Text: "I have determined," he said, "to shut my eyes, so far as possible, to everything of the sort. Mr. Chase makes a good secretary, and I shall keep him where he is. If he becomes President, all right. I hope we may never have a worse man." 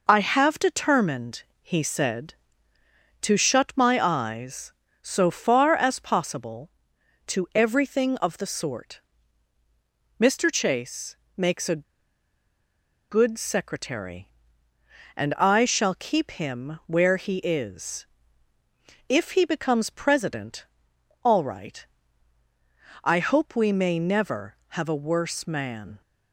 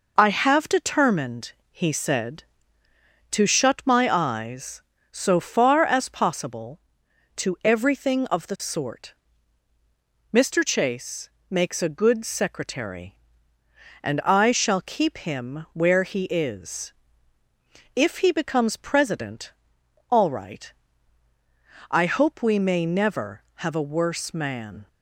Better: second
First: pauses between "Chase" and "makes"; slight; at 11.1 s; 0.22 s long // pauses between "a" and "good"; strong; at 11.8 s; 1.2 s long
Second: pauses between "Chase" and "makes"; slight; at 11.2 s; 0.22 s long

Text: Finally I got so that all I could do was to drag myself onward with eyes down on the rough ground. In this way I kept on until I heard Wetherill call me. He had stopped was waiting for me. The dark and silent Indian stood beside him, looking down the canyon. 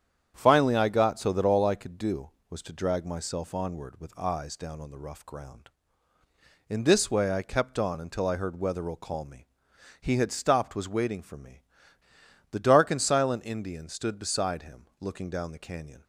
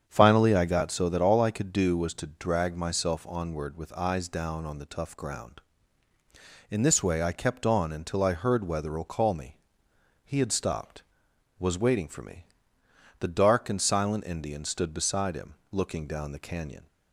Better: first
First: starts louder than the rest; strong; until 1.3 s; 8.5 dB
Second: starts louder than the rest; strong; until 1.0 s; 8 dB // says "tough" for "rough"; at 4.8 s

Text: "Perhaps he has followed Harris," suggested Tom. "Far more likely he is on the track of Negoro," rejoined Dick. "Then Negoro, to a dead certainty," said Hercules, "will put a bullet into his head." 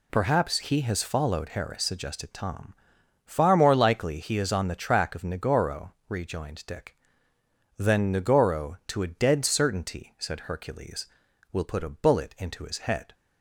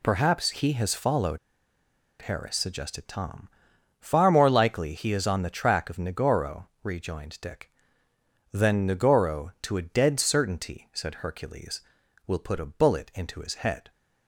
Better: first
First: none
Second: pauses between "followed" and "Harris"; noticeable; at 1.3 s; 0.83 s long

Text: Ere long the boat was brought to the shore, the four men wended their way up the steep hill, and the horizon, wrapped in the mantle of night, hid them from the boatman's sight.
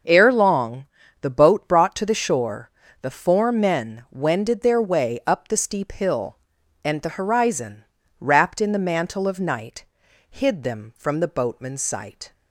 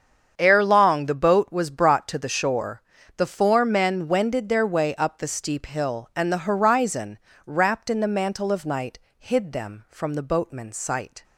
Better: second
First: starts louder than the rest; until 1.4 s; 7 dB // pauses between "long" and "the"; at 0.8 s; 0.38 s long // skips "was"; at 1.6 s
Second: starts louder than the rest; strong; until 1.3 s; 7.5 dB

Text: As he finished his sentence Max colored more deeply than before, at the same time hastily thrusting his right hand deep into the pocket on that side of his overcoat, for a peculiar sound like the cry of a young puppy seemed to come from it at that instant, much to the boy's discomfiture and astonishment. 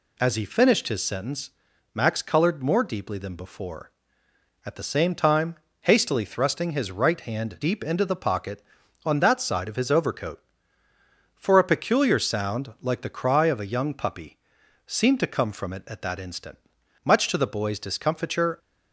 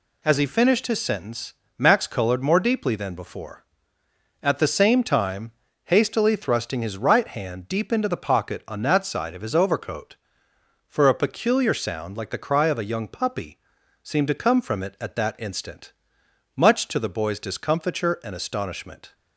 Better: second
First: pauses between "sentence" and "Max"; at 1.5 s; 0.44 s long // pauses between "time" and "hastily"; slight; at 5.5 s; 0.26 s long // pauses between "puppy" and "seemed"; noticeable; at 14.3 s; 0.48 s long // stops before "and astonishment"; at 18.5 s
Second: pauses between "sentence" and "Max"; slight; at 1.5 s; 0.24 s long // pauses between "time" and "hastily"; slight; at 5.5 s; 0.32 s long // pauses between "puppy" and "seemed"; at 13.5 s; 0.44 s long

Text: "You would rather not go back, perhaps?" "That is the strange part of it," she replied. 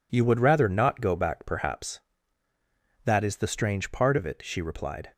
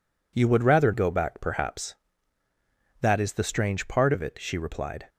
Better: first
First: none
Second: skips "not"; at 0.9 s

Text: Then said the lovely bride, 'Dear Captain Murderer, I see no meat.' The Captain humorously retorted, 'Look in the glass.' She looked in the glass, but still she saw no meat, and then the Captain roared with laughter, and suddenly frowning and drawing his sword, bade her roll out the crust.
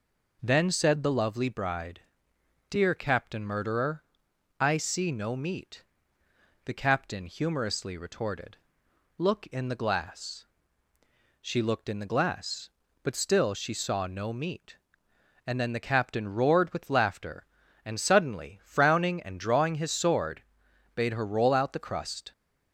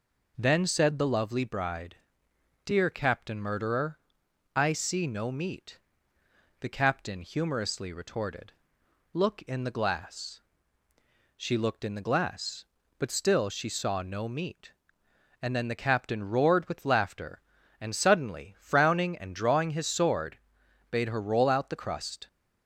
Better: neither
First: none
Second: none

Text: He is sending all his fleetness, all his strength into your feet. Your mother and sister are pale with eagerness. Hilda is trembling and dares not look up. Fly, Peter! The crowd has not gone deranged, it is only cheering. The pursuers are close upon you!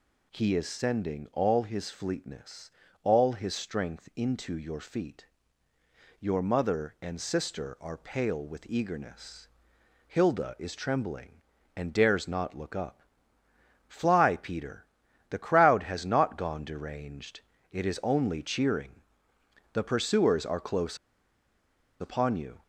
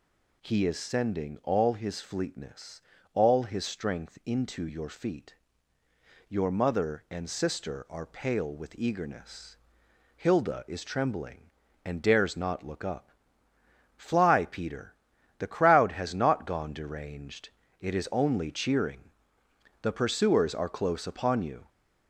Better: second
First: pauses between "close" and "upon"; at 20.9 s; 1.0 s long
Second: none

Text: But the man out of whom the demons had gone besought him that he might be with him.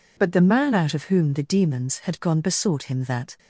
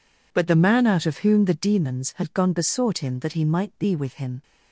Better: second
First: stops before "he might be with him"; at 3.3 s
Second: none

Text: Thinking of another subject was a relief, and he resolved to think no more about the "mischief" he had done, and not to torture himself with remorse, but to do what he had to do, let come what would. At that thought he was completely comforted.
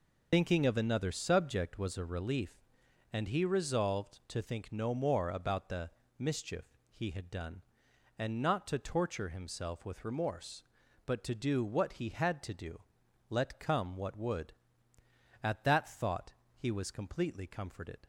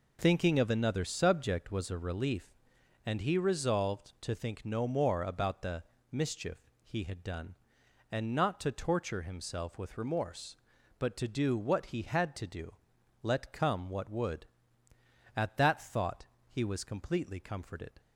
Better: second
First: loses the start of "Thinking"; at 0.3 s; 70 ms // pauses between "the" and "mischief"; slight; at 5.8 s; 0.30 s long // pauses between "mischief" and "he"; slight; at 6.6 s; 0.26 s long // pauses between "thought" and "he"; slight; at 16.3 s; 0.24 s long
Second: pauses between "the" and "mischief"; slight; at 5.8 s; 0.30 s long // pauses between "mischief" and "he"; slight; at 6.5 s; 0.26 s long // pauses between "thought" and "he"; slight; at 16.2 s; 0.24 s long

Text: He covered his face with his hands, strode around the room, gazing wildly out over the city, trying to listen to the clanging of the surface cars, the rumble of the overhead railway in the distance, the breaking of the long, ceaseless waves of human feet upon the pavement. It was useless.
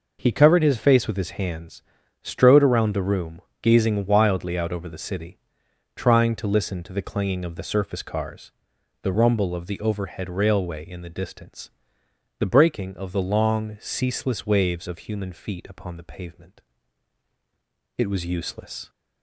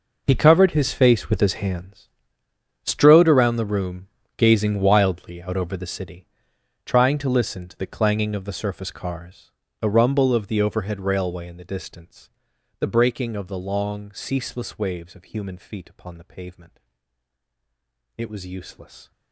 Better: first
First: none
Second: gets quieter; strong; throughout; 16.5 dB

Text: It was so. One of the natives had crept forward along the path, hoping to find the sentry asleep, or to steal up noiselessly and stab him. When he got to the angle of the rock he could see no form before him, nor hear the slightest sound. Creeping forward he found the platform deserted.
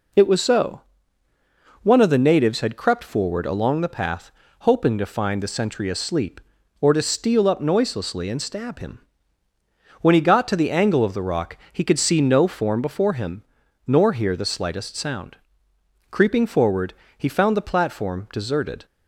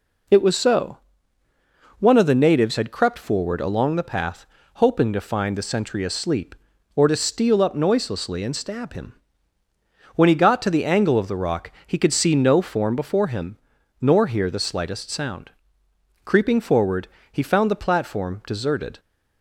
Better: neither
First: pauses between "forward" and "he"; slight; at 16.9 s; 0.24 s long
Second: pauses between "forward" and "he"; slight; at 17.0 s; 0.24 s long

